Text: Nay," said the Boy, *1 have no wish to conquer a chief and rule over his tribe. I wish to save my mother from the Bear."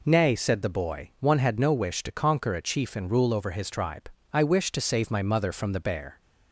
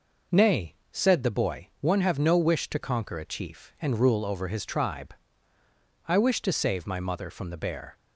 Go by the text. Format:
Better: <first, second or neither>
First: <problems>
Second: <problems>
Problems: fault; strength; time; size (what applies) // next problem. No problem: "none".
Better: second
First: says "had" for "have"; at 1.3 s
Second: none